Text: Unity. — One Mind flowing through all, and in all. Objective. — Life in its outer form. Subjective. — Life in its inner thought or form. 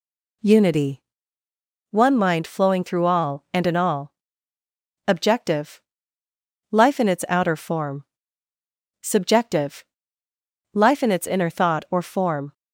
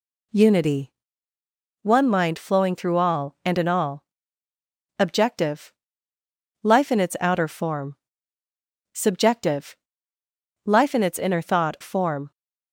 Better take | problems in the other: first | skips "or"; at 11.7 s

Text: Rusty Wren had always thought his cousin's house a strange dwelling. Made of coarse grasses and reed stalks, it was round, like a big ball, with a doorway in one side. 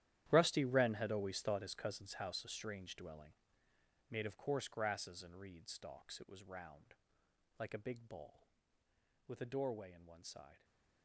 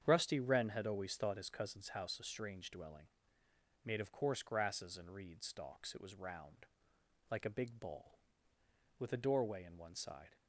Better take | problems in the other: second | gets quieter; strong; throughout; 17 dB // starts louder than the rest; strong; until 1.3 s; 12 dB; strong in the second

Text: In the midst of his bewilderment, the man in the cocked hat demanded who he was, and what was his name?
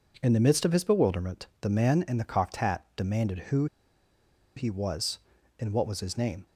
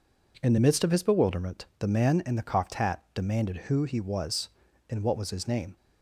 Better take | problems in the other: second | pauses between "who" and "he"; noticeable; at 3.6 s; 0.90 s long

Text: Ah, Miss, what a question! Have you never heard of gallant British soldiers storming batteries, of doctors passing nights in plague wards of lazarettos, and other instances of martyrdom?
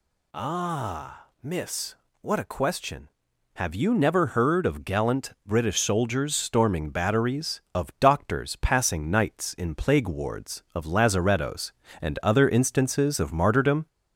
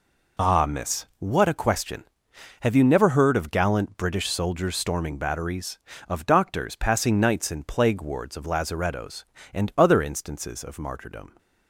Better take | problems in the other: second | gets louder; slight; throughout; 2 dB

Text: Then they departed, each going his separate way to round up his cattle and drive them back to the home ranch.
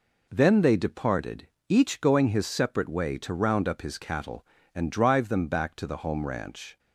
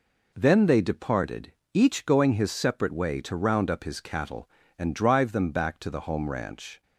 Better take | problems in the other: neither | none

